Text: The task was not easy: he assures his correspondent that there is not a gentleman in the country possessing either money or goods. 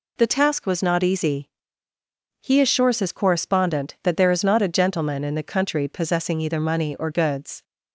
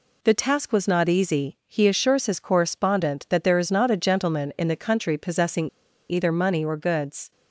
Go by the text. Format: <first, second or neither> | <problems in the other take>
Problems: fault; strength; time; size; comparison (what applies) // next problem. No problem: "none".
first | pauses between "possessing" and "either"; at 5.6 s; 0.41 s long